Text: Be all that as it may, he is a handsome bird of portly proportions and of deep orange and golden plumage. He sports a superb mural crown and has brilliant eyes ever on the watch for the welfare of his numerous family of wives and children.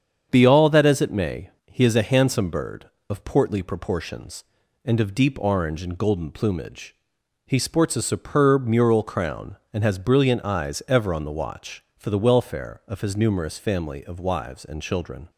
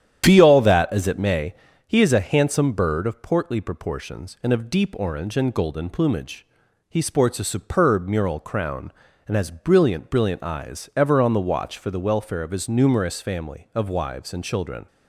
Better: first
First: starts louder than the rest; strong; until 1.3 s; 7.5 dB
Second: starts louder than the rest; strong; until 1.2 s; 10 dB // says "brilliant" twice; at 10.0 s

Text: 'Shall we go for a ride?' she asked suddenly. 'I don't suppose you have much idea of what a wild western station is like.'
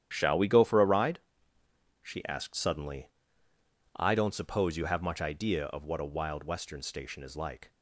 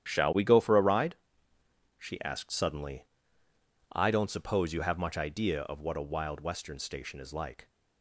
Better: neither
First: starts louder than the rest; strong; until 1.1 s; 10.5 dB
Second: starts louder than the rest; strong; until 1.1 s; 10.5 dB

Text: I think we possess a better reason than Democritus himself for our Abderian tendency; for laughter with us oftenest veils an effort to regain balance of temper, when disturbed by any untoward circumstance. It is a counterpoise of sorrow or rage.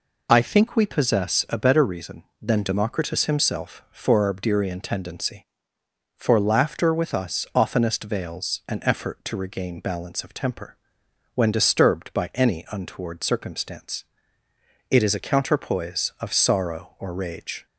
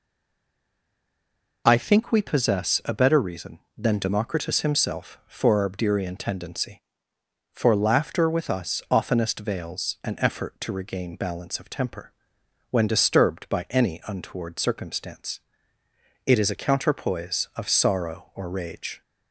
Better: first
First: none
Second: stays silent before the first word; noticeable; until 1.6 s; 1.6 s long

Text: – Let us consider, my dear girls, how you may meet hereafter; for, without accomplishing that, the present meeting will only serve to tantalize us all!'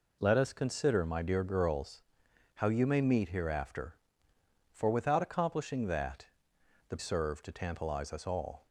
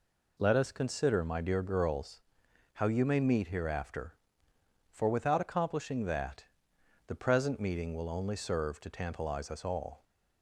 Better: second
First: skips "present meeting will only"; at 6.9 s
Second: none

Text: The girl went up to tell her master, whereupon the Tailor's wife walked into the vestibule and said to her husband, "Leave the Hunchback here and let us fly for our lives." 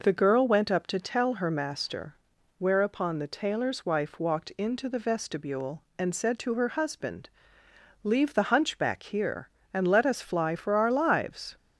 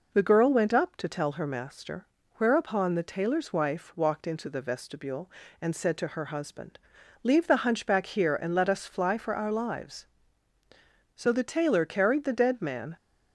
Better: first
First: none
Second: goes on to say "So the Tailor carried the dead man"; strong; from 11.1 s on; 1.7 s long

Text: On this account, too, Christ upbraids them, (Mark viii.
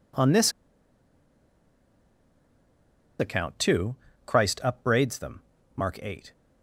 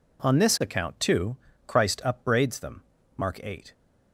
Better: second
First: pauses between "this" and "account"; strong; at 0.5 s; 2.6 s long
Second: none

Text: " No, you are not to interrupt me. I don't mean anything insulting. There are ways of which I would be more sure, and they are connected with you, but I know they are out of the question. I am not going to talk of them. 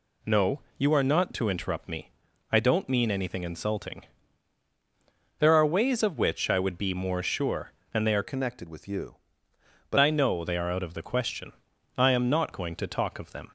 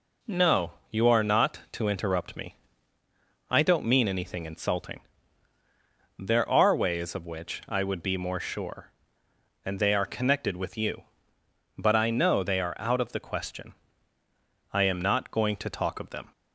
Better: second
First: changes voice from "connected" to "but"; from 8.2 to 9.9 s; 1.7 s long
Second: none

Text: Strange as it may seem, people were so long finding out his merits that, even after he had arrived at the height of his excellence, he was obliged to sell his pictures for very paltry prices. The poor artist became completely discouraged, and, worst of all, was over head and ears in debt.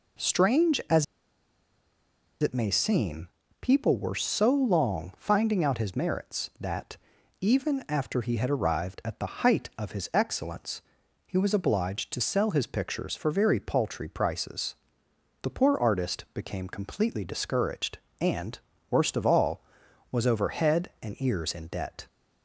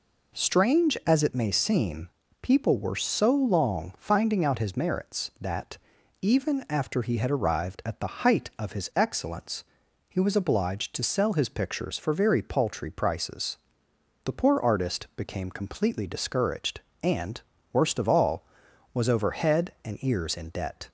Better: second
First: pauses between "as" and "it"; strong; at 1.0 s; 1.3 s long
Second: none

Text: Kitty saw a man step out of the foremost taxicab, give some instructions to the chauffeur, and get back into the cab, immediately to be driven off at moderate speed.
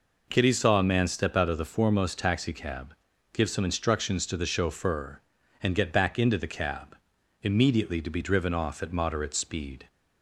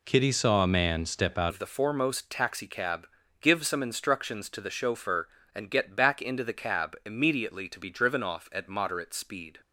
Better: first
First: none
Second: changes voice at "of"; from 1.4 s on; 8.2 s long

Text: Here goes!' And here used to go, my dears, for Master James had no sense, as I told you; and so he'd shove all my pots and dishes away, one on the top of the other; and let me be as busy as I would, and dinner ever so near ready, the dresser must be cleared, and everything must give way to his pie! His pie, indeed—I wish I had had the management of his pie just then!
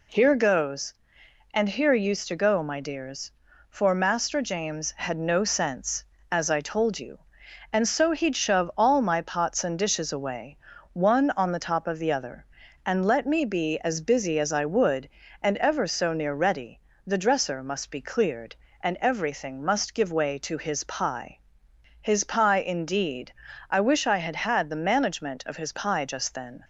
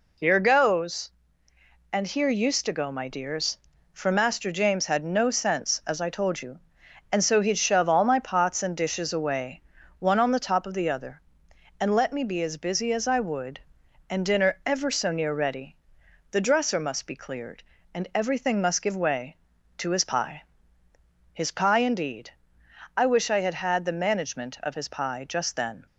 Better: second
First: skips "dinner"; at 15.5 s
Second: none

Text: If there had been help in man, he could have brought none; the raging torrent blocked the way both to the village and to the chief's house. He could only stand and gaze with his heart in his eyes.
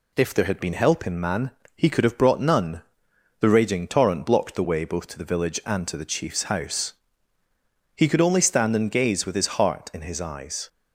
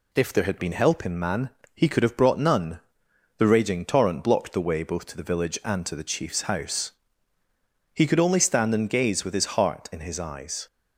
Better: neither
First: none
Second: none

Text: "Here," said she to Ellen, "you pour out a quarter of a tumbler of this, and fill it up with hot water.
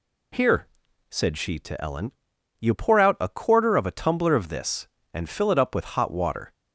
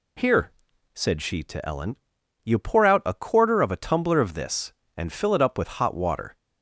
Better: neither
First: none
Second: none

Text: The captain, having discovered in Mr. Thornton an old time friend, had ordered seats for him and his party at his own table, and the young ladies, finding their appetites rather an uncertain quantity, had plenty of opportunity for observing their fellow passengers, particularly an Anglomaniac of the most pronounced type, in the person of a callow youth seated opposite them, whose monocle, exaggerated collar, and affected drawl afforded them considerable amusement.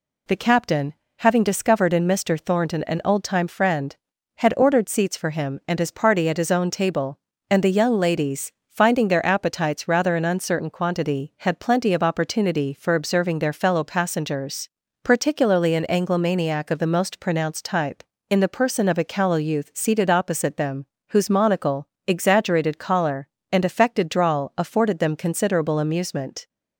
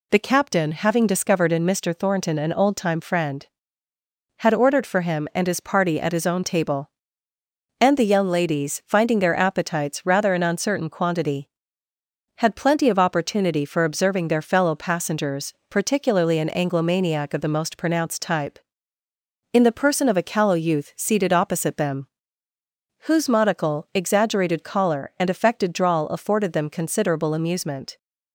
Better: first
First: none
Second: skips "seats"; at 4.8 s

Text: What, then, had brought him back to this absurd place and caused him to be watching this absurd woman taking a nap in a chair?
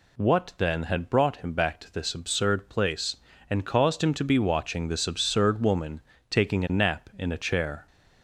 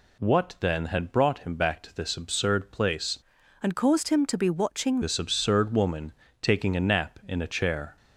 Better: first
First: pauses between "woman" and "taking"; slight; at 6.0 s; 0.30 s long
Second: changes voice from "and" to "watching"; from 3.6 to 4.9 s; 1.3 s long // pauses between "woman" and "taking"; slight; at 6.1 s; 0.30 s long

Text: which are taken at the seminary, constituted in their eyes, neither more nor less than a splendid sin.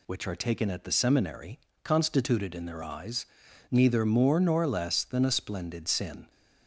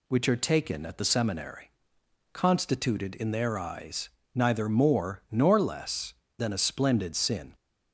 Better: neither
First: none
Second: none

